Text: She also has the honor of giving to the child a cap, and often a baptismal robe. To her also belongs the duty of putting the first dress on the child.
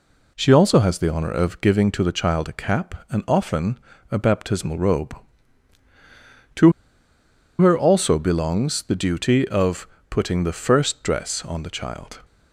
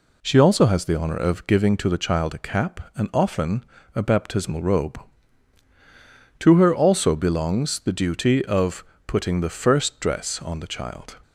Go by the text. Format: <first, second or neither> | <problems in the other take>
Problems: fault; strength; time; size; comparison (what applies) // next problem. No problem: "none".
second | pauses between "often" and "a"; slight; at 3.7 s; 0.32 s long; slight in the second // pauses between "To" and "her"; noticeable; at 6.7 s; 0.87 s long // pauses between "of" and "putting"; slight; at 9.8 s; 0.22 s long; slight in the second